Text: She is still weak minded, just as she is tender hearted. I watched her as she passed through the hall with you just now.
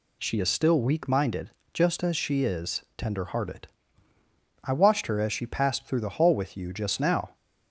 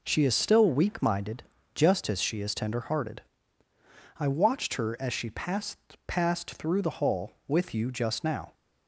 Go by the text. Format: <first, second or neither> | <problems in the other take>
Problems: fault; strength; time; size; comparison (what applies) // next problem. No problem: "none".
first | says "passed" twice; at 6.0 s